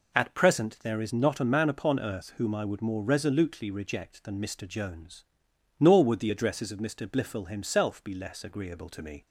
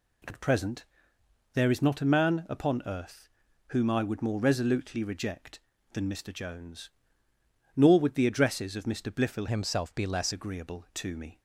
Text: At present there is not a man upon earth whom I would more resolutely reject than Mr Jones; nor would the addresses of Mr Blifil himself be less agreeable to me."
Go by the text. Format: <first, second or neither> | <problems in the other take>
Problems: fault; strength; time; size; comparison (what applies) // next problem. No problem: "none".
first | pauses between "present" and "there"; noticeable; at 0.8 s; 0.68 s long // pauses between "earth" and "whom"; at 3.2 s; 0.40 s long // changes voice from "himself" to "less"; from 9.4 to 10.3 s; 0.9 s long